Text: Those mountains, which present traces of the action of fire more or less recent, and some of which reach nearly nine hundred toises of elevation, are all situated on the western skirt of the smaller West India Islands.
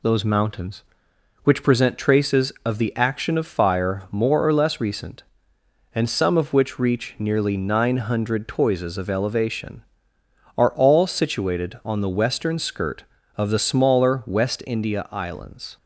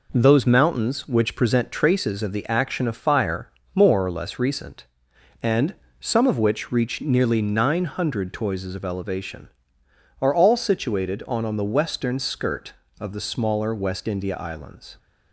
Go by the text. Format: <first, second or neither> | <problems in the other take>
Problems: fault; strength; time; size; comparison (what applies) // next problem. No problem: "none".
first | pauses between "fire" and "more"; slight; at 3.4 s; 0.26 s long // pauses between "and" and "some"; slight; at 5.7 s; 0.28 s long // says "on" twice; at 11.4 s